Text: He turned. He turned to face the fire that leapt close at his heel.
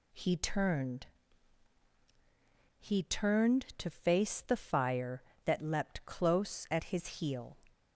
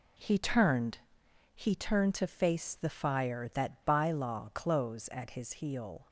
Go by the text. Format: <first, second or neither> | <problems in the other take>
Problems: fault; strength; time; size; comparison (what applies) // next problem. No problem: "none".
first | says "bylaw" for "leapt"; at 3.8 s